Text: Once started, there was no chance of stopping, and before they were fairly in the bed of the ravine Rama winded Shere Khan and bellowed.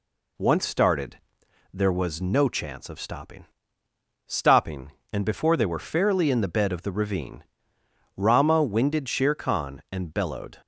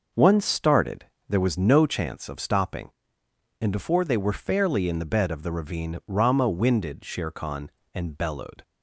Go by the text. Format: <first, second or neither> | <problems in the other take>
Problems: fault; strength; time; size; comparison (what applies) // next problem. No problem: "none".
second | says "stopping" twice; at 4.2 s // pauses between "ravine" and "Rama"; noticeable; at 7.4 s; 0.72 s long